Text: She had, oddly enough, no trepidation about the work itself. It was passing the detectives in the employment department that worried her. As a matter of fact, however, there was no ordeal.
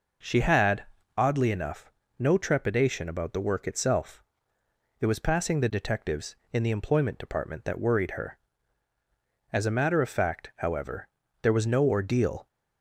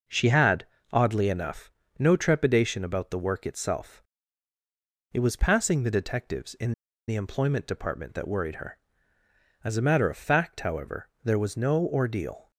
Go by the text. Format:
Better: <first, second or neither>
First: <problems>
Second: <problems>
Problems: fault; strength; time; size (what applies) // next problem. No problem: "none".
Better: first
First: none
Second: pauses between "in" and "the"; slight; at 6.7 s; 0.35 s long